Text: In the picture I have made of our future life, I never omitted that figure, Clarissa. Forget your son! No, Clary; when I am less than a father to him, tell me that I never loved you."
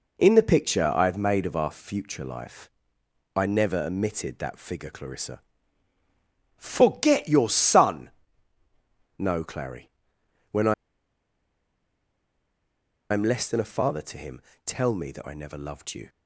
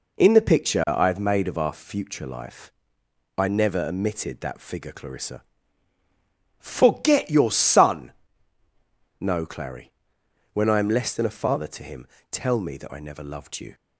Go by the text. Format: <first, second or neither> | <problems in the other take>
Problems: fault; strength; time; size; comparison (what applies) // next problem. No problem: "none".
second | pauses between "I" and "am"; strong; at 10.7 s; 2.3 s long